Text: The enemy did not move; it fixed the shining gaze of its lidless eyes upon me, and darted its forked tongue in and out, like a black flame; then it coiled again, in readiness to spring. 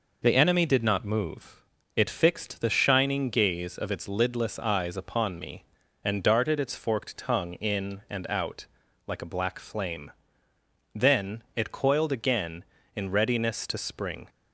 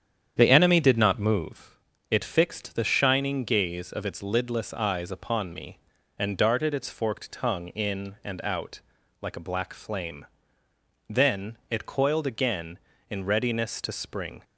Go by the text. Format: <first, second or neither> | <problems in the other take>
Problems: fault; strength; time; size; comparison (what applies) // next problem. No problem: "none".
first | starts louder than the rest; strong; until 1.5 s; 9 dB